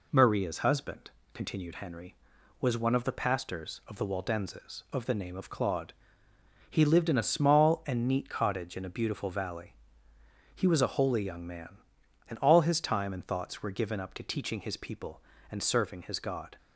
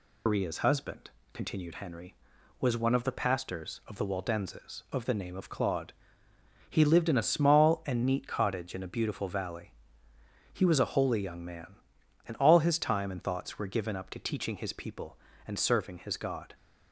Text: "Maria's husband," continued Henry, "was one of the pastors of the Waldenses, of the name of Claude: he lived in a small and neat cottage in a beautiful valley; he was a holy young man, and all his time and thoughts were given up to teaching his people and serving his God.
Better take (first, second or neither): first